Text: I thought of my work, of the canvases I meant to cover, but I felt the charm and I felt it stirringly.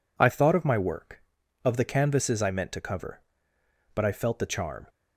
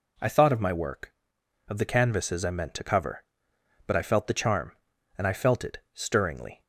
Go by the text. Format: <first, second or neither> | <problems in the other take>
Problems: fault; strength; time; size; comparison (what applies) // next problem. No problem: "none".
second | stops before "and I felt it stirringly"; at 4.8 s